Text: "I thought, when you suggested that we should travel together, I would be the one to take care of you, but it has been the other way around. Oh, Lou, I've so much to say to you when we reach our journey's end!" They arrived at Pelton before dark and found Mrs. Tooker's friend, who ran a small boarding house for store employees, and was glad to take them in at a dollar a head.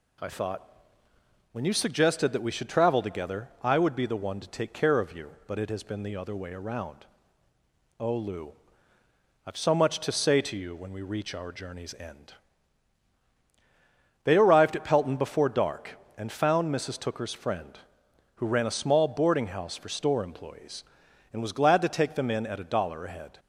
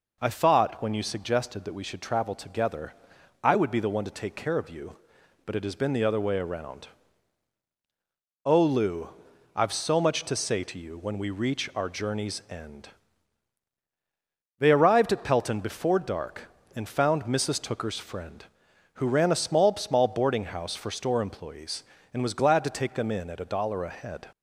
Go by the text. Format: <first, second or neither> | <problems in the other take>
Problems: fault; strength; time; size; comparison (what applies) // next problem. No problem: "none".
first | says "small" twice; at 19.7 s